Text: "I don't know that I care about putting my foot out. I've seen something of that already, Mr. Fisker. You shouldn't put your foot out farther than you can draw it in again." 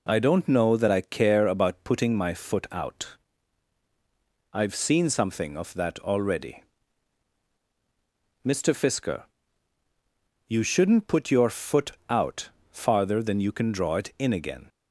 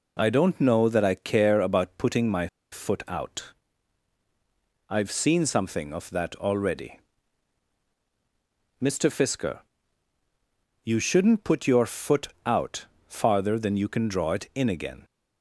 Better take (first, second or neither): first